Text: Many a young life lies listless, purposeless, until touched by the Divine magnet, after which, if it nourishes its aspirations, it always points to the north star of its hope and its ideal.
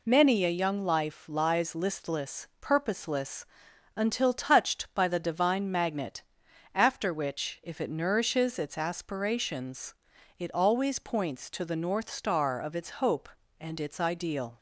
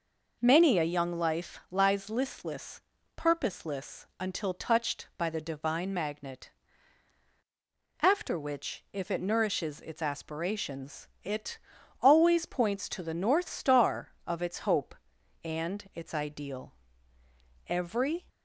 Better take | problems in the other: first | pauses between "it" and "always"; at 11.5 s; 0.42 s long // goes on to say "Every"; noticeable; from 17.6 s on; 0.62 s long

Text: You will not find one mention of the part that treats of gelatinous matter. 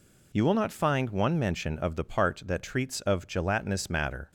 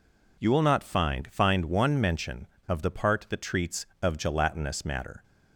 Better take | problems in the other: first | says "find" twice; at 1.3 s

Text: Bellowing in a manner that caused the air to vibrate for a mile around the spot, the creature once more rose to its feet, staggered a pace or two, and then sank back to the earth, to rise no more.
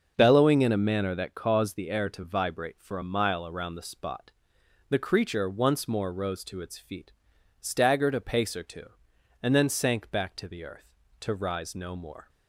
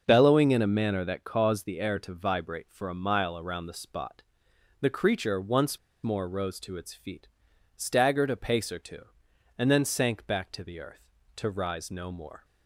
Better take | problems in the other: first | starts louder than the rest; until 1.1 s; 6.5 dB; also in the first // pauses between "once" and "more"; slight; at 5.7 s; 0.25 s long

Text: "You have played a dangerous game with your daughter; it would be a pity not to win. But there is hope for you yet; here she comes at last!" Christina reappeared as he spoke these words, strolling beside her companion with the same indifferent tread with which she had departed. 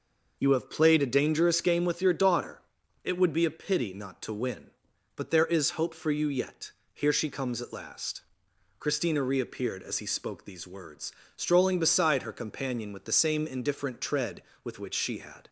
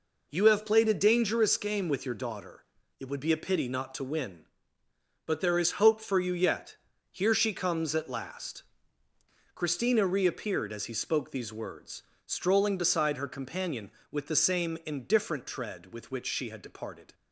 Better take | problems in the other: second | stops before "departed"; at 15.4 s

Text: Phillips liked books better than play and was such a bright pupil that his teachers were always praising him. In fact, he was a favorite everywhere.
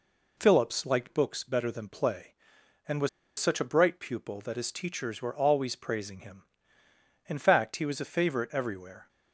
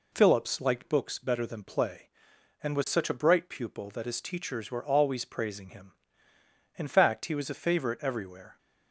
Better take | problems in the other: second | pauses between "was" and "such"; slight; at 3.0 s; 0.30 s long

